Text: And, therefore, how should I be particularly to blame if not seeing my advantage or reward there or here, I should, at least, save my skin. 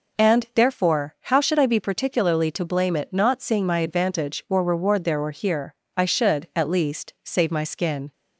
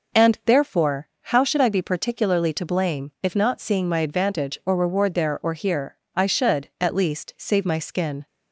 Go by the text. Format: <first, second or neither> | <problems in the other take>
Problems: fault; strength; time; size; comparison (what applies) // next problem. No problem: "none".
second | says "it" for "if"; at 2.9 s